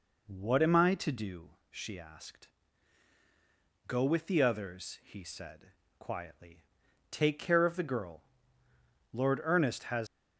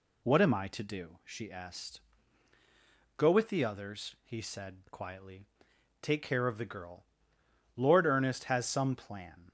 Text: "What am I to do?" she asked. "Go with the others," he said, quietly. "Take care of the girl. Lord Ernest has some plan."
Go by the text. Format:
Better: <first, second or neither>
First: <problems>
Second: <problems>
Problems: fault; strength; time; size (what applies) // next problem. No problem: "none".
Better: second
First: stops before "some plan"; at 10.0 s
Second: none